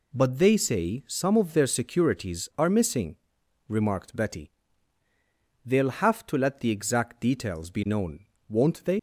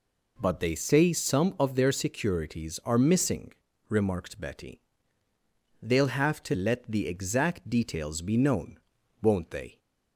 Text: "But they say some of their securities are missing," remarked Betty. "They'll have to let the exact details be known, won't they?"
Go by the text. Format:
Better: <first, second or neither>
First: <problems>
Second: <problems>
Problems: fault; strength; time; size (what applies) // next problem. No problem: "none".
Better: second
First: leaves "they" unfinished; at 8.9 s; 75 ms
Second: none